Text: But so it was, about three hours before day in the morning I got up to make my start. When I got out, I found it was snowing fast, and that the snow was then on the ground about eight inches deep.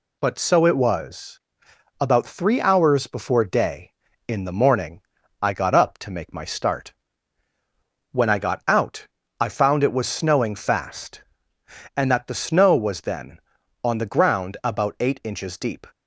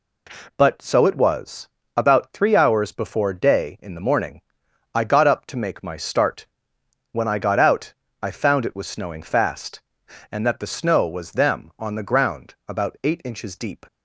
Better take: first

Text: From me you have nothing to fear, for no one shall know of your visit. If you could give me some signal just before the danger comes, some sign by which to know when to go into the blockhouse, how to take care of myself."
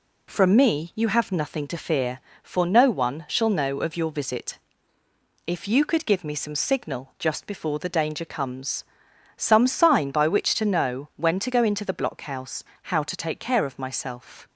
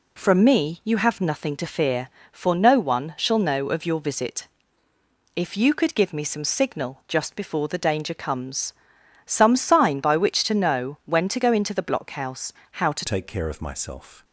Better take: first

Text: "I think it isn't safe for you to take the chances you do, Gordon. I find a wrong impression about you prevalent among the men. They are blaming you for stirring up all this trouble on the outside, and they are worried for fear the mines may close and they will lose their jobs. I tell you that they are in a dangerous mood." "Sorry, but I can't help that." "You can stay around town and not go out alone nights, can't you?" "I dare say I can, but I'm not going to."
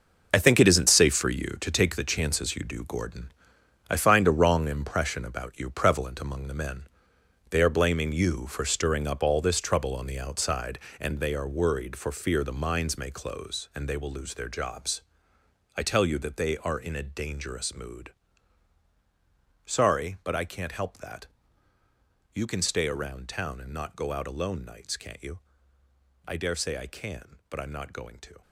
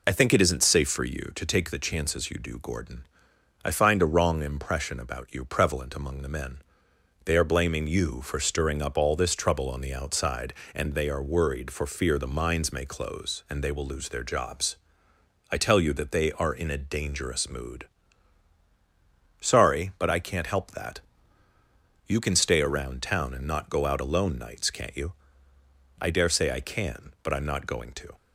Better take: second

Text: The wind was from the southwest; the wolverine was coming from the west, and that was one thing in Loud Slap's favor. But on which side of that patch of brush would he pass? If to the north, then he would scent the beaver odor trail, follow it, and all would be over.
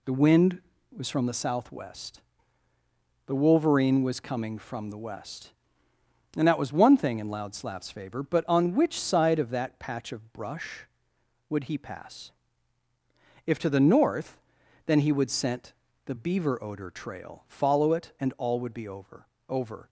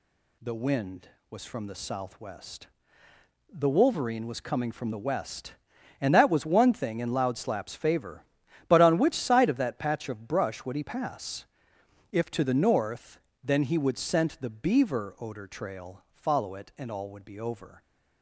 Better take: second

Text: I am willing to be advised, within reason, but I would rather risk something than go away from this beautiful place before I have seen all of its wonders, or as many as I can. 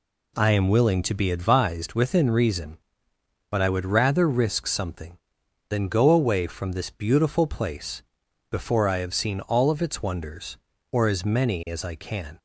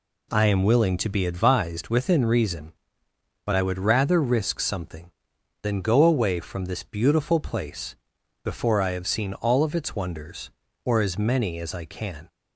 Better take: neither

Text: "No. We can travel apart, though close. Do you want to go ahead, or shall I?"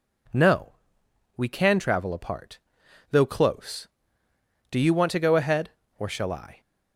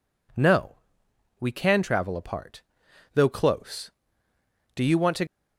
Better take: first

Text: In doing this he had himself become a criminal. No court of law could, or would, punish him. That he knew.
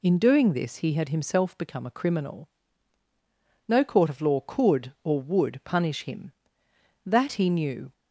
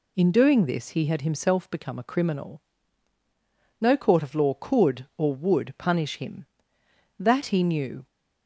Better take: neither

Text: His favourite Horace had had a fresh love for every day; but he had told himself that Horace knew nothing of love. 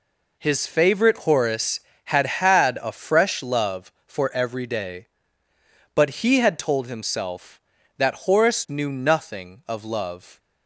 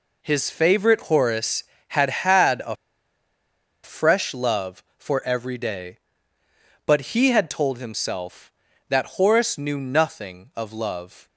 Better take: first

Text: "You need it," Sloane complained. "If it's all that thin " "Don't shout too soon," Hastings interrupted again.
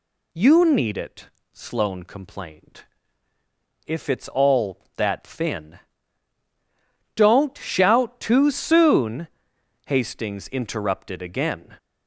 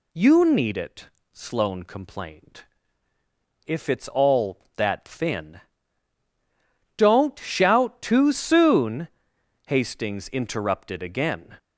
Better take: neither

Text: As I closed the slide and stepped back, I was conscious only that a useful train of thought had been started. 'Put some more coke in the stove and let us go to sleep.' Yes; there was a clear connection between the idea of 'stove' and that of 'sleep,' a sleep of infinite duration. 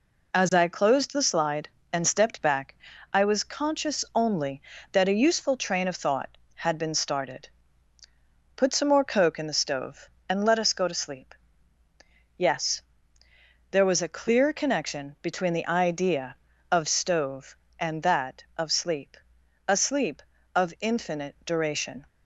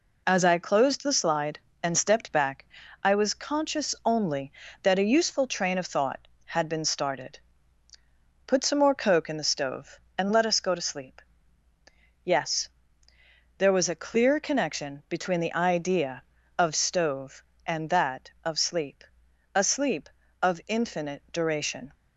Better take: neither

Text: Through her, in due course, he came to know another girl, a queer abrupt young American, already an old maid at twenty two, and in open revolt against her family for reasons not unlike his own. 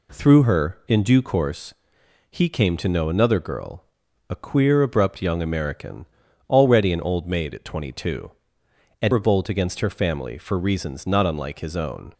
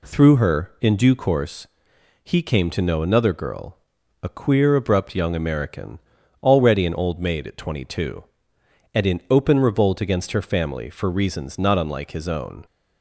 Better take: second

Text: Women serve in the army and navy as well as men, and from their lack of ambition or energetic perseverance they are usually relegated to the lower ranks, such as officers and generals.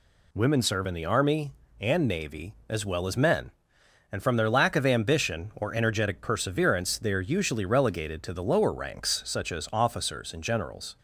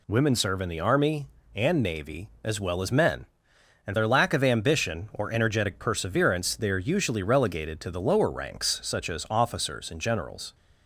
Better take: first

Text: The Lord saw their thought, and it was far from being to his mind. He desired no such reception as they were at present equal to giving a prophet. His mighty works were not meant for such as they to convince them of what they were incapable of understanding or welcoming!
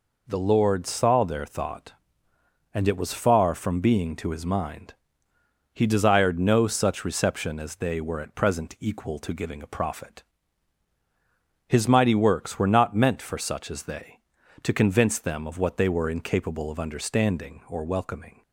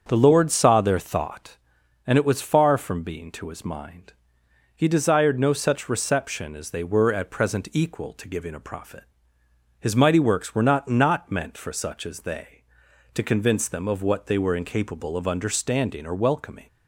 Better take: first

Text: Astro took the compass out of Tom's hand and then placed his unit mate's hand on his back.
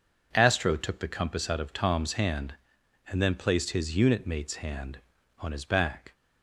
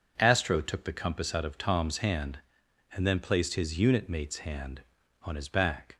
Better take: neither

